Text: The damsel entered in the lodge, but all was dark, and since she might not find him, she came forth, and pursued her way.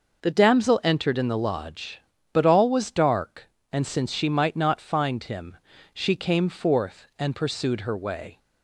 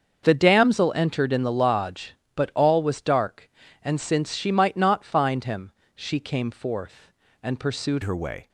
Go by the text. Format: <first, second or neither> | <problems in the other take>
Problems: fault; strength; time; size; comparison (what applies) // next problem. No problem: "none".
first | starts louder than the rest; until 1.3 s; 6.5 dB // changes voice at "her"; from 8.0 s on; 0.4 s long